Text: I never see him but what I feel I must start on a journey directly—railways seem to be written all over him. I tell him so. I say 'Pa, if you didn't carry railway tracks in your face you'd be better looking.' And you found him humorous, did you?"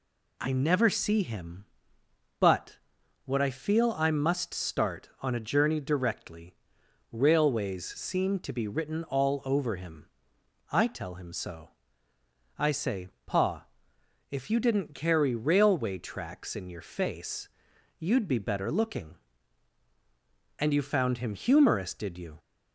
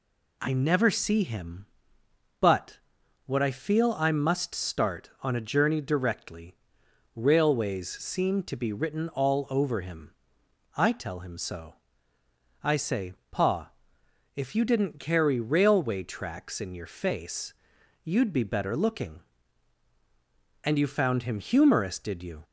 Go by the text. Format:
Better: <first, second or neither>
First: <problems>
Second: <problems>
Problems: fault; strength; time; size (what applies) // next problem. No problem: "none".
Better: neither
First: pauses between "but" and "what"; noticeable; at 2.7 s; 0.48 s long // pauses between "say" and "Pa"; slight; at 13.0 s; 0.16 s long // pauses between "face" and "you'd"; noticeable; at 17.4 s; 0.50 s long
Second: pauses between "but" and "what"; noticeable; at 2.7 s; 0.48 s long // pauses between "say" and "Pa"; slight; at 13.1 s; 0.16 s long // pauses between "face" and "you'd"; noticeable; at 17.5 s; 0.50 s long